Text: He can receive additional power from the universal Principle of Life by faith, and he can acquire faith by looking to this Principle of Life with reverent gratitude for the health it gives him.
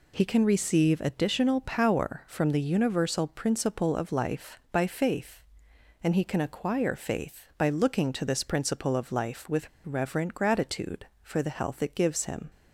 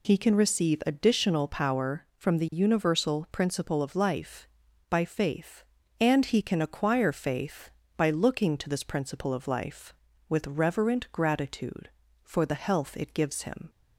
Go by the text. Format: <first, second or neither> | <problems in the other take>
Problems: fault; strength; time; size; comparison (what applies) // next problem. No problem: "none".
second | pauses between "with" and "reverent"; slight; at 9.6 s; 0.15 s long